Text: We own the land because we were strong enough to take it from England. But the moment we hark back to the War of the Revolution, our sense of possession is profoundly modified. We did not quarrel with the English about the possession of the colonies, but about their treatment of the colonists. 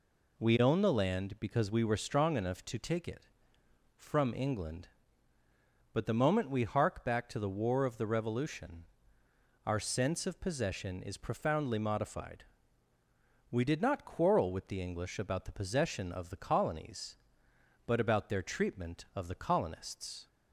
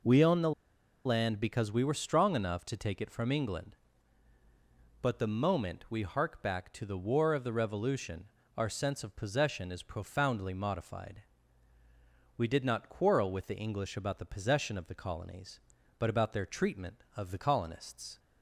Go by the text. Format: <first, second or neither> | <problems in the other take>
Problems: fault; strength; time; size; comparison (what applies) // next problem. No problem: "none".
first | pauses between "the" and "land"; noticeable; at 0.5 s; 0.54 s long